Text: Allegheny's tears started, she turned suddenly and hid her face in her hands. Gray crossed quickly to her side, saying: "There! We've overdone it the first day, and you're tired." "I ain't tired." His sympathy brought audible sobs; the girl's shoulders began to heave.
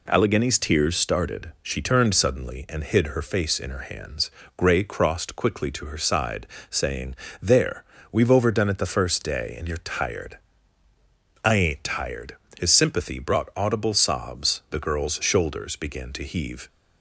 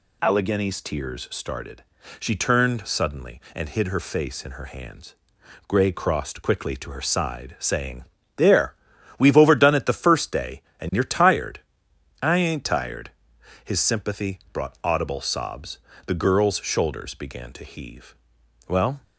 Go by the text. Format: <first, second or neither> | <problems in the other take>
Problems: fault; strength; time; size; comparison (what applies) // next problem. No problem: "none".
first | goes on to say "Well"; slight; from 18.6 s on; 0.34 s long